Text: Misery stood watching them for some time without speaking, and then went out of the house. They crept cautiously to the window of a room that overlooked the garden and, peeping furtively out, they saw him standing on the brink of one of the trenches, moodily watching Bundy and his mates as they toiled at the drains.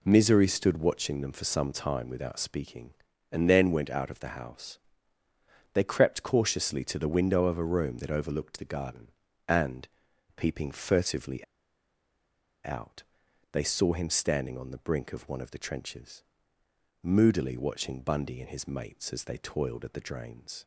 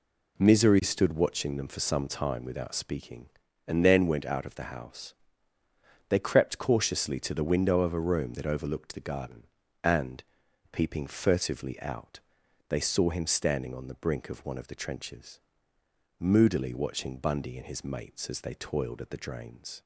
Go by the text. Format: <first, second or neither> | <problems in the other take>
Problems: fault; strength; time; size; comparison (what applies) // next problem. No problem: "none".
second | pauses between "furtively" and "out"; at 11.4 s; 1.2 s long